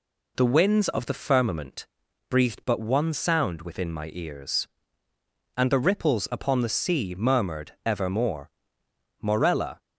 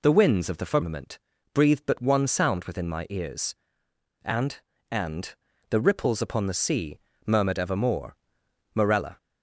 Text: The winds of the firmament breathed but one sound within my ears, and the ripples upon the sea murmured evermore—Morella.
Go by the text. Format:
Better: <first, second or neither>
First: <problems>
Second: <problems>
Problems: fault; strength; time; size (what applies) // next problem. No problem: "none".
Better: first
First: pauses between "firmament" and "breathed"; at 1.8 s; 0.42 s long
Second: pauses between "firmament" and "breathed"; slight; at 1.1 s; 0.36 s long // says "and" twice; at 4.9 s // pauses between "sea" and "murmured"; slight; at 6.9 s; 0.26 s long